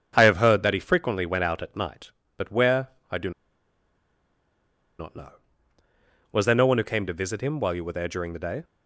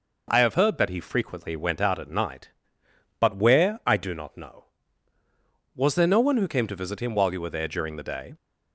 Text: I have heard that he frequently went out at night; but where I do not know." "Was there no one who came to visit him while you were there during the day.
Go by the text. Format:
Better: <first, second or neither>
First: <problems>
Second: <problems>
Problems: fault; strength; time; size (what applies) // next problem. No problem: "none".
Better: second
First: starts louder than the rest; strong; until 1.1 s; 7 dB // pauses between "where" and "I"; slight; at 2.8 s; 0.22 s long // pauses between "do" and "not"; strong; at 3.2 s; 1.6 s long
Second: none